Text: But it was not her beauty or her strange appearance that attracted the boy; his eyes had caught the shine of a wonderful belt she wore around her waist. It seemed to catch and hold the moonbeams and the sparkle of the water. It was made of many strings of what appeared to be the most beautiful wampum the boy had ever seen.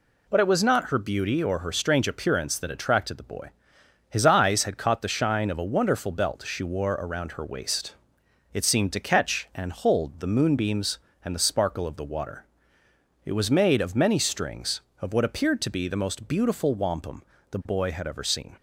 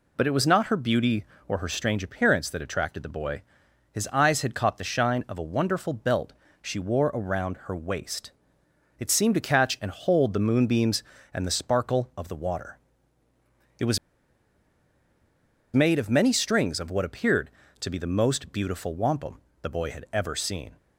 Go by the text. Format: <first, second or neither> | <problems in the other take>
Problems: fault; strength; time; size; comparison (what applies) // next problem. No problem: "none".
first | pauses between "belt" and "she"; slight; at 6.3 s; 0.28 s long // pauses between "was" and "made"; strong; at 13.9 s; 1.7 s long // pauses between "wampum" and "the"; slight; at 19.4 s; 0.22 s long; slight in the first